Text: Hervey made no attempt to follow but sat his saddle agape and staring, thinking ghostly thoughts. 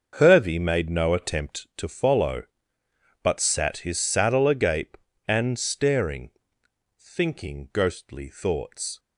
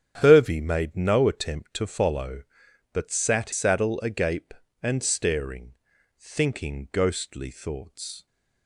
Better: first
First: starts louder than the rest; until 1.1 s; 6.5 dB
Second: starts louder than the rest; strong; until 1.2 s; 9 dB // skips "his"; at 3.5 s

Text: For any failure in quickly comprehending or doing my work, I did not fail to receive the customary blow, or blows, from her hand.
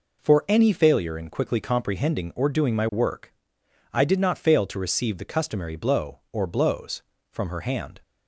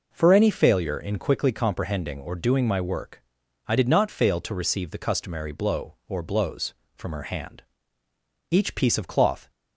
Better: first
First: none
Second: goes on to say "Each piece of cloth"; noticeable; from 8.5 s on; 1.0 s long

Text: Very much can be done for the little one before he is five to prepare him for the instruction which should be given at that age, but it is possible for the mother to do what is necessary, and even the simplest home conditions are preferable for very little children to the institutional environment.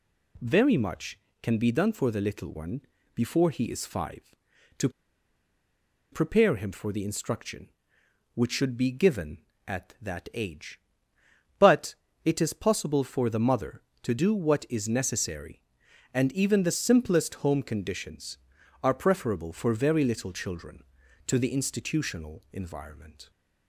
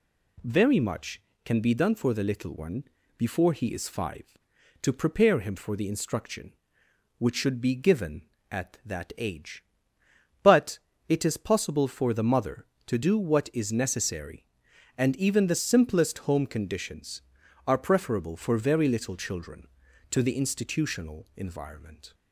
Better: second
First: pauses between "one" and "before"; slight; at 2.8 s; 0.32 s long // pauses between "to" and "prepare"; at 4.9 s; 1.2 s long // pauses between "but" and "it"; slight; at 11.9 s; 0.30 s long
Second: pauses between "one" and "before"; slight; at 2.8 s; 0.32 s long // pauses between "but" and "it"; slight; at 10.7 s; 0.30 s long

